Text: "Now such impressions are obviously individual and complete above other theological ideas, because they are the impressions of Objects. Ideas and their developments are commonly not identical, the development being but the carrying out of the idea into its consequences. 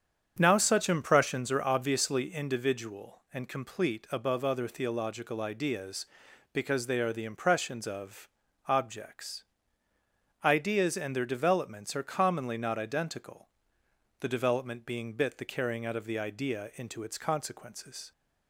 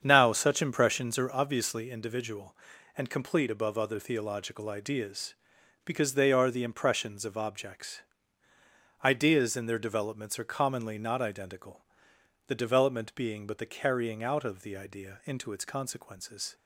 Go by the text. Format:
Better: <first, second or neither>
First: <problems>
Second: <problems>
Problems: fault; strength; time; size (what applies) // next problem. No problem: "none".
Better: second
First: starts louder than the rest; strong; until 1.4 s; 8 dB // pauses between "of" and "Objects"; at 8.2 s; 0.38 s long // says "bit" for "but"; at 15.1 s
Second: starts louder than the rest; strong; until 1.0 s; 7.5 dB